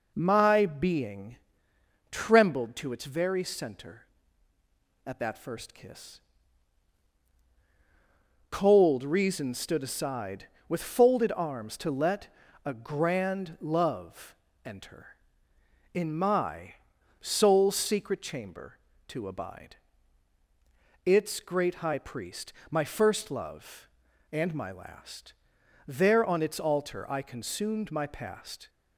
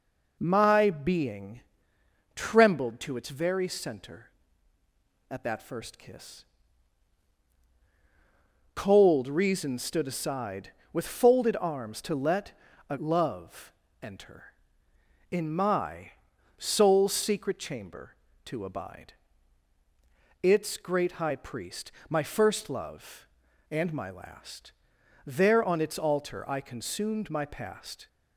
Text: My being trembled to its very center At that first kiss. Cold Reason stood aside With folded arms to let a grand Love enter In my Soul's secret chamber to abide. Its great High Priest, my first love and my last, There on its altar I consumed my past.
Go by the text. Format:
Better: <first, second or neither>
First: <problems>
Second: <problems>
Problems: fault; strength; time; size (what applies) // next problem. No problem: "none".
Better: first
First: pauses between "being" and "trembled"; noticeable; at 1.3 s; 0.74 s long // pauses between "let" and "a"; slight; at 12.2 s; 0.36 s long // pauses between "Love" and "enter"; slight; at 14.3 s; 0.28 s long // pauses between "my" and "Soul's"; noticeable; at 16.7 s; 0.46 s long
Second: pauses between "being" and "trembled"; noticeable; at 1.6 s; 0.74 s long // pauses between "let" and "a"; slight; at 12.5 s; 0.36 s long // skips "grand"; at 12.9 s // pauses between "Love" and "enter"; slight; at 13.7 s; 0.28 s long // pauses between "my" and "Soul's"; noticeable; at 16.1 s; 0.46 s long